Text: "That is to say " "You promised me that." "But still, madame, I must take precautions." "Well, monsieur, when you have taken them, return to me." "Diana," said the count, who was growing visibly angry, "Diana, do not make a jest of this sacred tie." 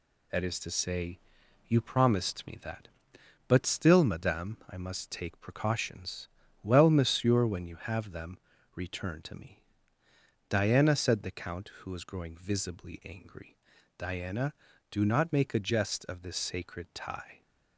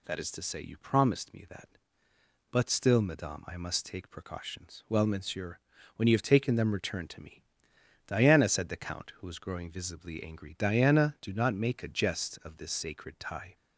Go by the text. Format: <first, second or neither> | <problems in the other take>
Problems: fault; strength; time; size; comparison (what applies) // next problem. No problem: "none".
second | skips "taken"; at 8.0 s